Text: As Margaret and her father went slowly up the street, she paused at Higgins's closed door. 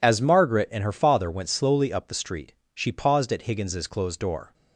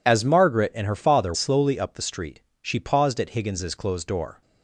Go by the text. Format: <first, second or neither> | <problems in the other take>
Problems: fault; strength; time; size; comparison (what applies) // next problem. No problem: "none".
first | skips "went"; at 1.3 s